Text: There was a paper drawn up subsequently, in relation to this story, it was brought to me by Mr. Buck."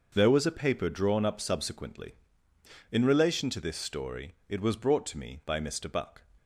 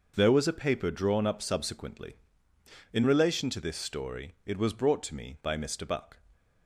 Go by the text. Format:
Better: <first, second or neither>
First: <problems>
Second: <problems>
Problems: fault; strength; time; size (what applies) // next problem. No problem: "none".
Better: neither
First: none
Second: none